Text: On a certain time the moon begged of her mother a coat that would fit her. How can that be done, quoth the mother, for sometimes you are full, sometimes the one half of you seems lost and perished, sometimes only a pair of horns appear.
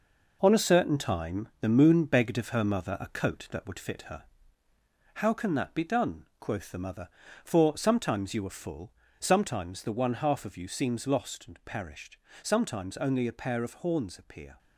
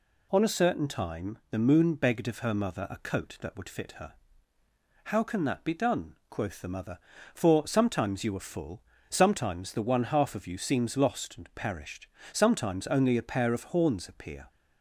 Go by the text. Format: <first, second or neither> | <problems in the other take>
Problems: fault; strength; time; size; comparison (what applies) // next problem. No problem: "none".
second | gets quieter; strong; throughout; 7.5 dB